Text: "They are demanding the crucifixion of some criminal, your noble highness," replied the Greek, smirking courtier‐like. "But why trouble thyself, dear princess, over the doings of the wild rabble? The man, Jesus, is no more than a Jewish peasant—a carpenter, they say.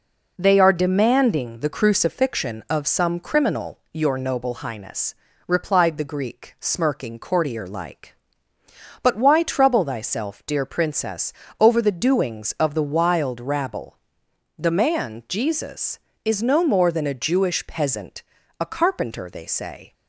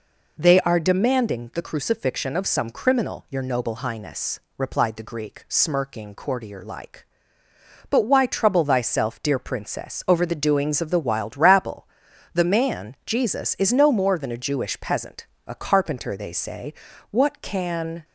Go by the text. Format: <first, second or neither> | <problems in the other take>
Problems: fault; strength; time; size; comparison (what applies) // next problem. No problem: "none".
first | goes on to say "What can"; noticeable; from 17.1 s on; 0.94 s long